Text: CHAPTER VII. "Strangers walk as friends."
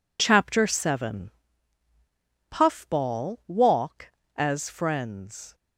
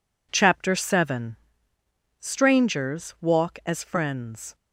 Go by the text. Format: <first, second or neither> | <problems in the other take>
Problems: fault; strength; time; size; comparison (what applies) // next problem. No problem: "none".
second | says "Puffball" for "Strangers"; at 2.5 s